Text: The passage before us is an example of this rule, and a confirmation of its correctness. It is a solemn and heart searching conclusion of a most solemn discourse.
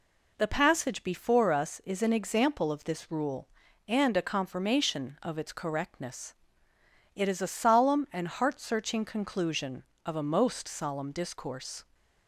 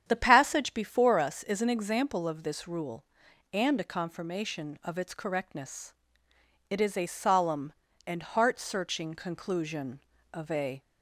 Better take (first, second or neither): first